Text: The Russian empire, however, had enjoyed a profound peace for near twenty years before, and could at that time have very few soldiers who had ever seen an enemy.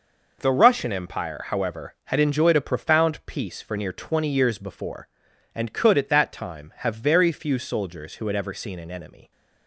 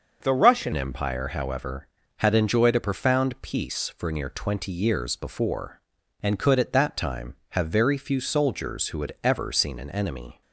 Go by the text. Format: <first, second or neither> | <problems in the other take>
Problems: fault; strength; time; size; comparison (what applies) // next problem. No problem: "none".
first | starts louder than the rest; until 1.2 s; 6.5 dB // changes voice at "empire"; from 0.7 s on; 9.7 s long